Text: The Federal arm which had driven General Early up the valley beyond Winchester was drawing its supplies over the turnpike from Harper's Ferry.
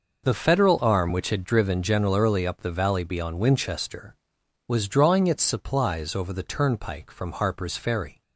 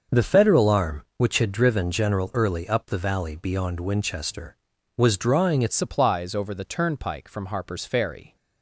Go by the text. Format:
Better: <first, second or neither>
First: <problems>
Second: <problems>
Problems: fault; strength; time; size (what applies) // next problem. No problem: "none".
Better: first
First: none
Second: starts louder than the rest; until 1.2 s; 6.5 dB // changes voice at "supplies"; from 5.7 s on; 2.6 s long